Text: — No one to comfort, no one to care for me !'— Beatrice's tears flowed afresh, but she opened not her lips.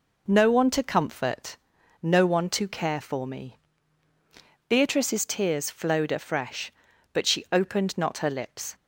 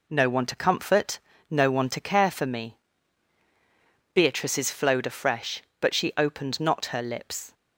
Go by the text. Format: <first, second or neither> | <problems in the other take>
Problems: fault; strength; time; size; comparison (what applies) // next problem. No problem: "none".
first | skips "tears"; at 4.6 s